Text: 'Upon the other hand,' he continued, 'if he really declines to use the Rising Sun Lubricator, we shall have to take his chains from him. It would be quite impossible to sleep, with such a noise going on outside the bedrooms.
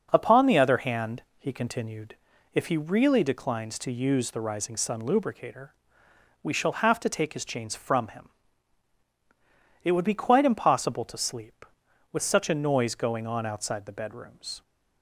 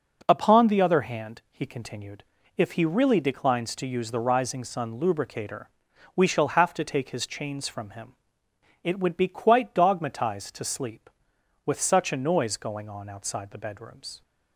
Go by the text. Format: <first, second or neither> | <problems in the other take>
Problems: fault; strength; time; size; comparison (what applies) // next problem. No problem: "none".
first | says "dogmatized" for "impossible"; at 9.7 s